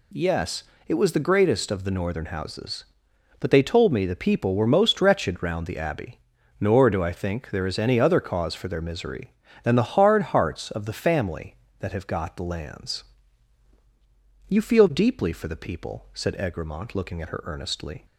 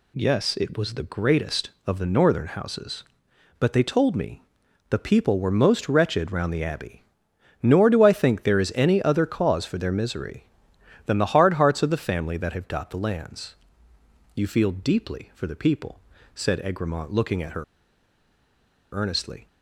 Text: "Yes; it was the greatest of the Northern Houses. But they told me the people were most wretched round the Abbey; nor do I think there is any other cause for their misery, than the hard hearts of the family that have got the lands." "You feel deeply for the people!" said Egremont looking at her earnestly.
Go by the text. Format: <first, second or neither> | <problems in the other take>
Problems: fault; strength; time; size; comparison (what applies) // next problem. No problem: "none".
first | pauses between "me" and "the"; noticeable; at 4.4 s; 0.48 s long // pauses between "her" and "earnestly"; strong; at 17.6 s; 1.2 s long